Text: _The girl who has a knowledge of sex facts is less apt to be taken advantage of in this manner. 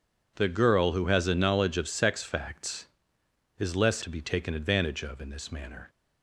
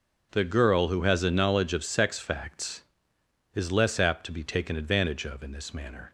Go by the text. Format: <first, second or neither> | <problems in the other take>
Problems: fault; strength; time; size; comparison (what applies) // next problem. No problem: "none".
second | skips "apt"; at 4.0 s